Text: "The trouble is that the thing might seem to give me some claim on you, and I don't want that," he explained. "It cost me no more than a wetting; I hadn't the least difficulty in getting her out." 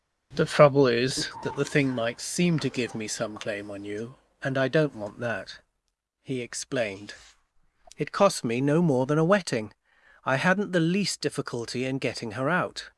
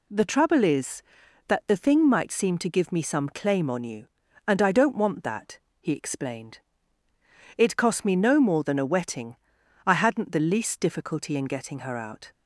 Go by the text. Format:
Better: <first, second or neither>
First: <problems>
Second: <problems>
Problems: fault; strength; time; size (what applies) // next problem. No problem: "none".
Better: second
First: starts louder than the rest; noticeable; until 1.6 s; 5.5 dB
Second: none